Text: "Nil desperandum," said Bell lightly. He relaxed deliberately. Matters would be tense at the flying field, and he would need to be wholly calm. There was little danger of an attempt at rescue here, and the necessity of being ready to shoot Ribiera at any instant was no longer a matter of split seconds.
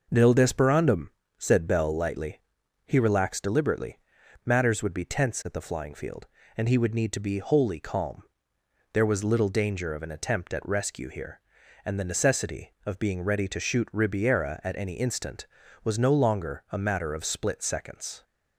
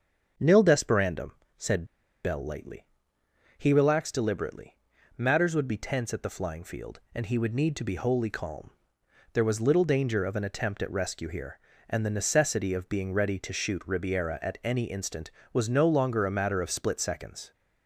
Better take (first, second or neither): first